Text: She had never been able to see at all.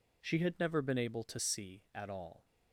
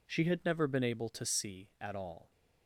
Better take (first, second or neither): neither